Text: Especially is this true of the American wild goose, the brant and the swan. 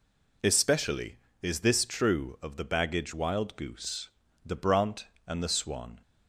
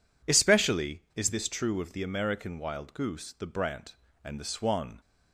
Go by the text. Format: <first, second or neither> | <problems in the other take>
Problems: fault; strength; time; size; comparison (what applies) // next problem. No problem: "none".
second | says "Baggage" for "American"; at 2.6 s